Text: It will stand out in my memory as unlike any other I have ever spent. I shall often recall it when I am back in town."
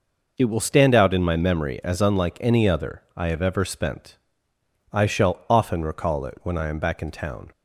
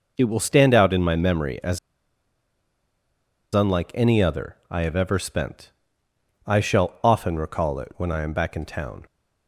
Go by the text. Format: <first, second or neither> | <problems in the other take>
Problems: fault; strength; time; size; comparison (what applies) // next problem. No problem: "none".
first | pauses between "as" and "unlike"; strong; at 1.7 s; 1.7 s long